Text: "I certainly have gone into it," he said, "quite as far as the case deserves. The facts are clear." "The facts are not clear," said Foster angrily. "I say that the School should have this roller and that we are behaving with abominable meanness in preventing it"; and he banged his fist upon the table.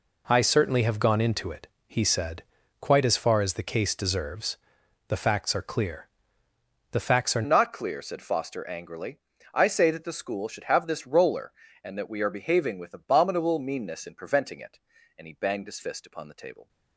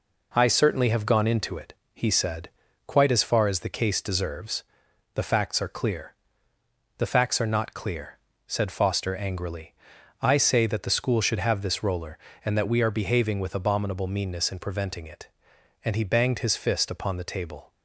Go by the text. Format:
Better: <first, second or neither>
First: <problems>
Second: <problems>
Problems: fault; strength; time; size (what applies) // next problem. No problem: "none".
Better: second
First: changes voice at "not"; from 7.4 s on; 9.2 s long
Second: none